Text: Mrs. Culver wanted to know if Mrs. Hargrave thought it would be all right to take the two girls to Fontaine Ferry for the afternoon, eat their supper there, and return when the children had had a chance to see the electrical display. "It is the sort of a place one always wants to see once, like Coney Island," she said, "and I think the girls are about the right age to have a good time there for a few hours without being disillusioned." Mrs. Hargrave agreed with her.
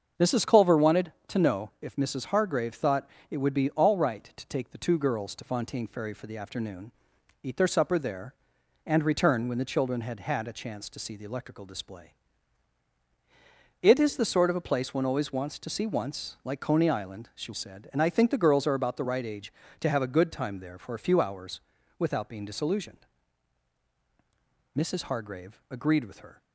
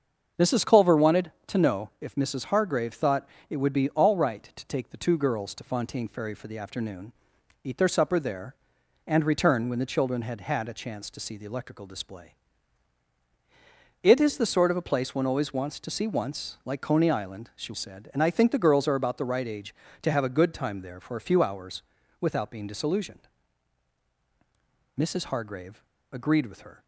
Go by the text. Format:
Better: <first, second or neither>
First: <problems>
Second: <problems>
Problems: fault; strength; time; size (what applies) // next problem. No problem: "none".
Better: first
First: starts louder than the rest; until 1.3 s; 6.5 dB // pauses between "thought" and "it"; slight; at 3.0 s; 0.22 s long // pauses between "hours" and "without"; at 21.5 s; 0.38 s long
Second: starts louder than the rest; until 1.5 s; 6.5 dB // pauses between "thought" and "it"; slight; at 3.2 s; 0.22 s long // pauses between "hours" and "without"; at 21.8 s; 0.38 s long // pauses between "Hargrave" and "agreed"; slight; at 25.8 s; 0.31 s long